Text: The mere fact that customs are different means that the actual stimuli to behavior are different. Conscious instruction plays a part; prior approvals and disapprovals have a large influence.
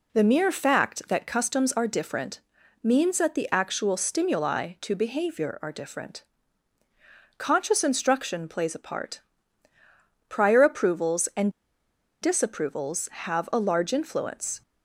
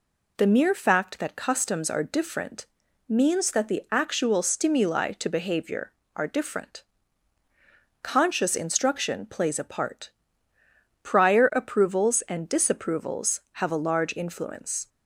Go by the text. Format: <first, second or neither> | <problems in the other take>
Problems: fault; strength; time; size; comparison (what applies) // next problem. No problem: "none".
second | pauses between "different" and "means"; at 2.3 s; 0.42 s long; also in the second // pauses between "and" and "disapprovals"; noticeable; at 11.5 s; 0.70 s long